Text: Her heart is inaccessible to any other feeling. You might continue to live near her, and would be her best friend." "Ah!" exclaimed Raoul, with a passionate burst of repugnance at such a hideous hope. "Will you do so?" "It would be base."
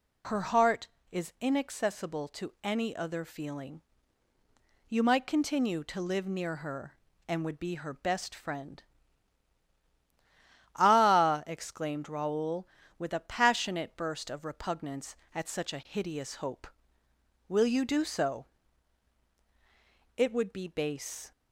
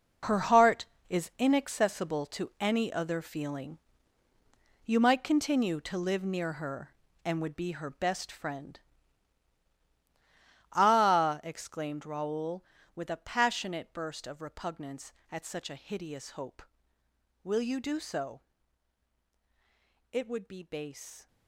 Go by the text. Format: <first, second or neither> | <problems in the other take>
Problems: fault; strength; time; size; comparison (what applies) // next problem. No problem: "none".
first | gets quieter; strong; throughout; 12.5 dB